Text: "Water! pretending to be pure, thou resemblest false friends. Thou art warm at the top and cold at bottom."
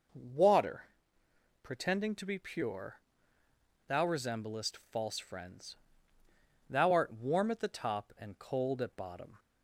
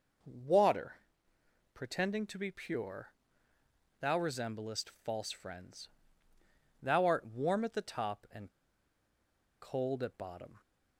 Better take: first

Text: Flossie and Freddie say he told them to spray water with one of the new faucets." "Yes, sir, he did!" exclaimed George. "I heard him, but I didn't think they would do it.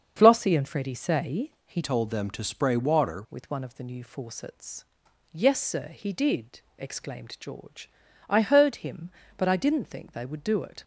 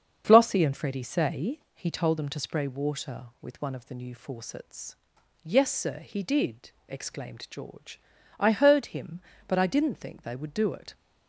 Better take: second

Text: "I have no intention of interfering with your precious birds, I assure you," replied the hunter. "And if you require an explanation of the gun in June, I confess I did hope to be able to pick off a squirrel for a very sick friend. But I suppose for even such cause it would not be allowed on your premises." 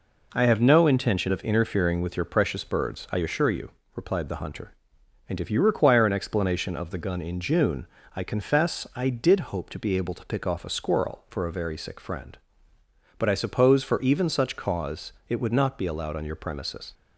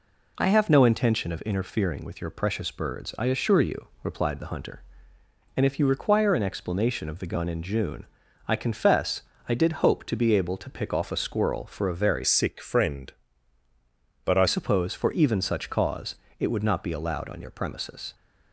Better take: first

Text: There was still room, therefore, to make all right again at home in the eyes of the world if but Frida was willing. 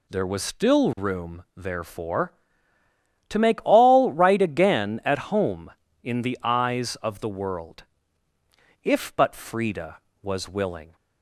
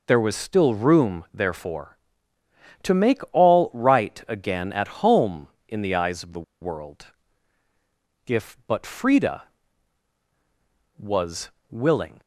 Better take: first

